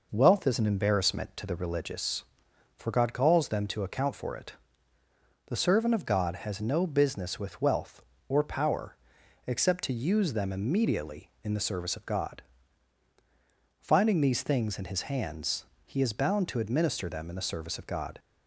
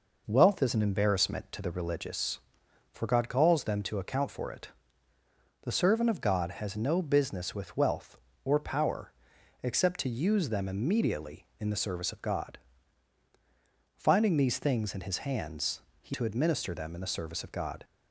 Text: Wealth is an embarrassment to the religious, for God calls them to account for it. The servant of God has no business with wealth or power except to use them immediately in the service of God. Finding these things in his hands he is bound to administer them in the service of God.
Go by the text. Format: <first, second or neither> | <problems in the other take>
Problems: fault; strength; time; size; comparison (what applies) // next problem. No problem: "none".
first | pauses between "power" and "except"; noticeable; at 9.1 s; 0.48 s long; noticeable in the first // pauses between "hands" and "he"; slight; at 15.8 s; 0.18 s long; slight in the first // skips "is bound"; at 16.1 s